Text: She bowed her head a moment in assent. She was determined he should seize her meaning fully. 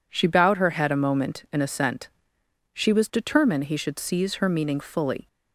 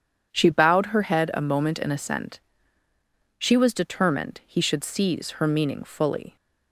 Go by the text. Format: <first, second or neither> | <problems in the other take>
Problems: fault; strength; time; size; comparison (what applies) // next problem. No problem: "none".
neither | none